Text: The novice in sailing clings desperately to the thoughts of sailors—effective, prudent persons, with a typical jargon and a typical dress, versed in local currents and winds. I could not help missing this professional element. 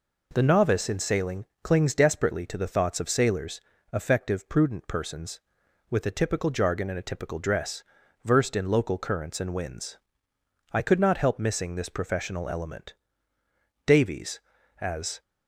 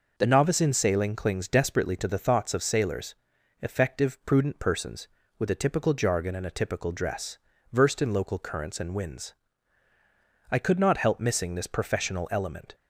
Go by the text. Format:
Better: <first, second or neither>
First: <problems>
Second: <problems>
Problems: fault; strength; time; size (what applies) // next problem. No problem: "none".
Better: second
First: pauses between "sailing" and "clings"; slight; at 1.4 s; 0.18 s long // goes on to say "Davies as"; from 13.8 s on; 1.3 s long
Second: none